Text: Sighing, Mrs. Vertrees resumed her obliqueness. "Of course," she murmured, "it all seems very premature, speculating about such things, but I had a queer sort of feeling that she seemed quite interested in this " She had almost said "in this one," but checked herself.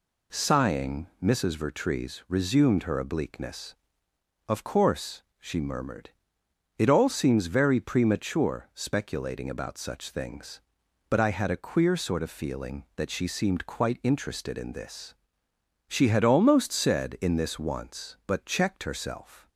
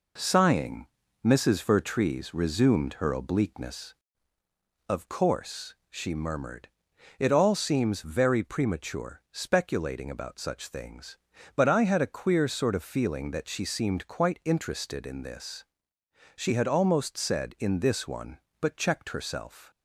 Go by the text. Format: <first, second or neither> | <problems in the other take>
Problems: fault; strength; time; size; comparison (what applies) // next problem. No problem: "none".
second | says "once" for "one"; at 17.5 s